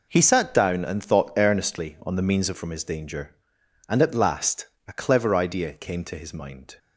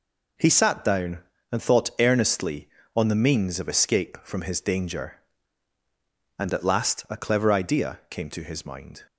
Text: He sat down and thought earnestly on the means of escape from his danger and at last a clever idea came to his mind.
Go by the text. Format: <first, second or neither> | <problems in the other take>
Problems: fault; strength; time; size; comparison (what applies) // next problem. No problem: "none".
second | skips "escape"; at 2.5 s // pauses between "last" and "a"; slight; at 4.6 s; 0.22 s long